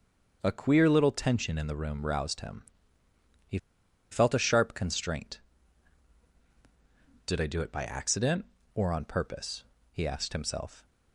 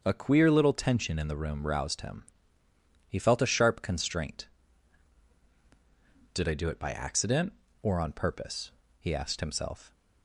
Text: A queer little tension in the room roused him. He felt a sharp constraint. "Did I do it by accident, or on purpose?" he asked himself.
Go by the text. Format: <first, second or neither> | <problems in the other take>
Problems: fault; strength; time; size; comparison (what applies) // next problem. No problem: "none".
second | starts louder than the rest; until 1.4 s; 6.5 dB; also in the second // pauses between "He" and "felt"; noticeable; at 3.5 s; 0.53 s long